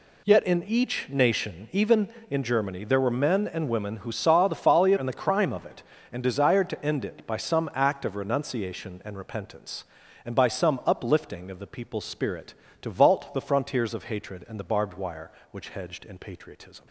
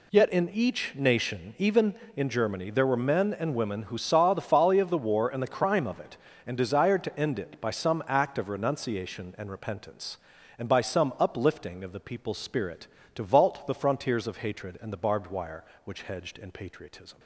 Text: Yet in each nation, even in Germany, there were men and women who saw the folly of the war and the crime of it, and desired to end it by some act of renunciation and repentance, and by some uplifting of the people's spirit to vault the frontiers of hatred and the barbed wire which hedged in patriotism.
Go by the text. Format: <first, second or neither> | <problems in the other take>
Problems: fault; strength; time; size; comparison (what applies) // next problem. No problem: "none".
second | skips "of the war"; at 4.9 s